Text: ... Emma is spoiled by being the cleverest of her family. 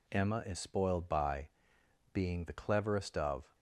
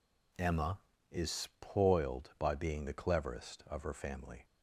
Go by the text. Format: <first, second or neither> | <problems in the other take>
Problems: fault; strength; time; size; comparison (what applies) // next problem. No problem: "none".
second | pauses between "by" and "being"; noticeable; at 1.4 s; 0.64 s long // stops before "her family"; at 3.5 s